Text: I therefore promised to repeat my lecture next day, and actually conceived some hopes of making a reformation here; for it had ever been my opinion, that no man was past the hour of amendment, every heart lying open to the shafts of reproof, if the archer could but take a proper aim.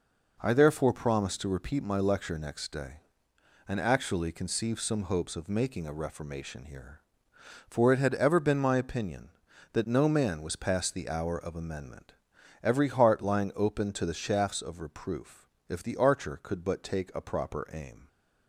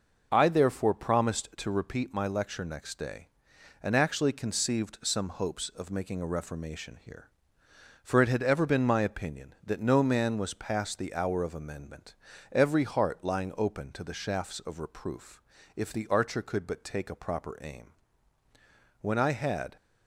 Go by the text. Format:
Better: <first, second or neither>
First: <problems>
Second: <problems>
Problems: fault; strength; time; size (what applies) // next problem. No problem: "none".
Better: first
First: none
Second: goes on to say "When I had"; noticeable; from 19.0 s on; 0.74 s long